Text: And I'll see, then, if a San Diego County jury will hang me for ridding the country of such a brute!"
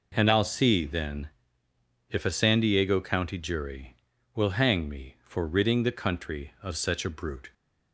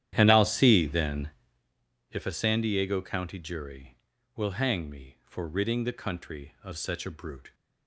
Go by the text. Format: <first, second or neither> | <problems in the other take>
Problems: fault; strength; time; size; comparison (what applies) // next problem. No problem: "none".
first | starts louder than the rest; strong; until 1.8 s; 11 dB